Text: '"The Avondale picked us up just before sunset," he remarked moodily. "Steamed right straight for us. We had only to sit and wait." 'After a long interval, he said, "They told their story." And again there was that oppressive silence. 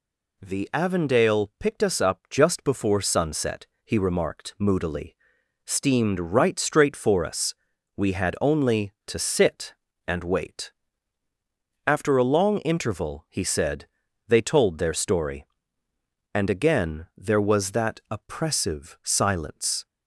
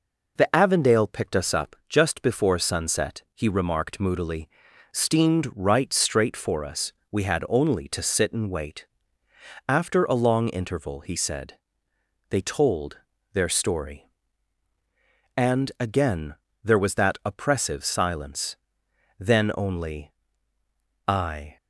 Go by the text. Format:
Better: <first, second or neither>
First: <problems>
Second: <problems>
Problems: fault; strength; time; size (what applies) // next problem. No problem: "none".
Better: first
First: none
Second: pauses between "told" and "their"; slight; at 12.9 s; 0.34 s long // pauses between "again" and "there"; slight; at 16.3 s; 0.28 s long // goes on to say "Then only I"; strong; from 19.1 s on; 2.3 s long